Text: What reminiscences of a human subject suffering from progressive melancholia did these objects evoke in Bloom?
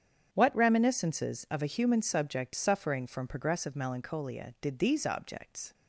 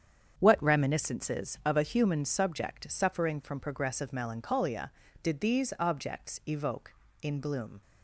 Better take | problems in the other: second | starts louder than the rest; strong; until 1.3 s; 8 dB; strong in the second // stops before "evoke in Bloom"; at 5.7 s

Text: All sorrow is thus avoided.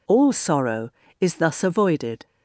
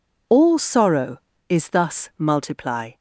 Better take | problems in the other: first | says "multiply" for "avoided"; at 2.1 s

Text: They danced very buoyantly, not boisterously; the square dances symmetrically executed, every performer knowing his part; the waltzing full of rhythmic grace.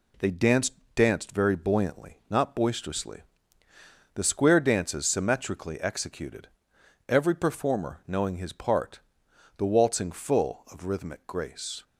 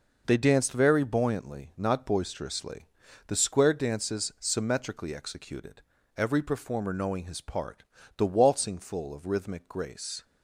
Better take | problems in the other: second | says "danced" twice; at 0.9 s

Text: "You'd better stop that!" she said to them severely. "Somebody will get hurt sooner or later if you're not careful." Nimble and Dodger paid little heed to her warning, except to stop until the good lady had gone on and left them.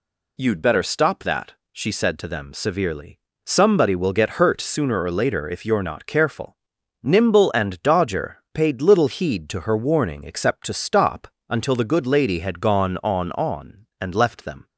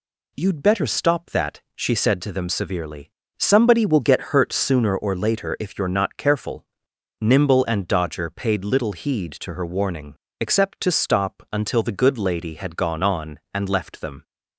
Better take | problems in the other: second | pauses between "stop" and "until"; slight; at 11.2 s; 0.22 s long // says "on" twice; at 13.3 s

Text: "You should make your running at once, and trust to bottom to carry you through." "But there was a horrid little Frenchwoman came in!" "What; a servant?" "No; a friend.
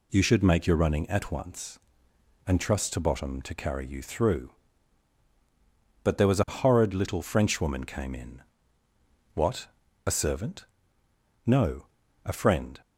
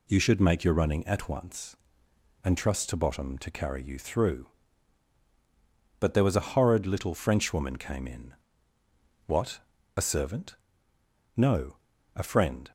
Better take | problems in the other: neither | none

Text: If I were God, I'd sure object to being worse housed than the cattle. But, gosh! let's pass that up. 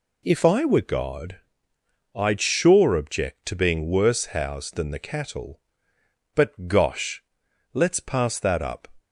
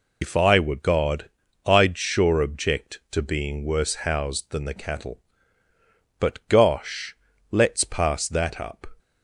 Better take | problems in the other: first | loses the start of "If"; at 0.2 s; 95 ms

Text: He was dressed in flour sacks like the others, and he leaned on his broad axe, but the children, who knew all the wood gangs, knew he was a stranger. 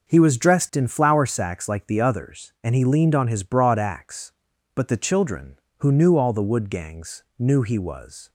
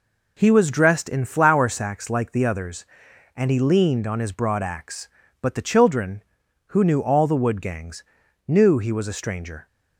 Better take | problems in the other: second | starts louder than the rest; until 1.1 s; 6.5 dB // stops before "a stranger"; at 8.2 s

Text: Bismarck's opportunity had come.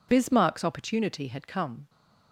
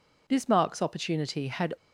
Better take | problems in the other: first | stops before "come"; at 1.7 s

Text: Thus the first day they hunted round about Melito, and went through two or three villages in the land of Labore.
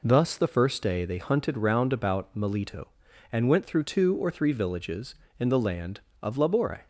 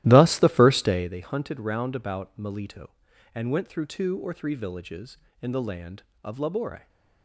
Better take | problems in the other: first | starts louder than the rest; strong; until 1.2 s; 14 dB

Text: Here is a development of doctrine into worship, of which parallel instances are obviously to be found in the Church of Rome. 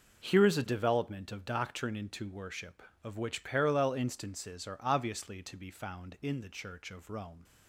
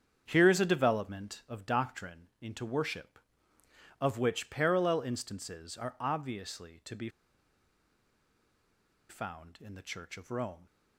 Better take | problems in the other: first | starts louder than the rest; strong; until 1.2 s; 8 dB // pauses between "be" and "found"; strong; at 7.0 s; 2.0 s long

